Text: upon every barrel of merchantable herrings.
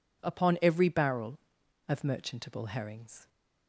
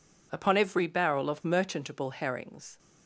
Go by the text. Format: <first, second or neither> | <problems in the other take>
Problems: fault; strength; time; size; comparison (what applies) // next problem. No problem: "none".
neither | none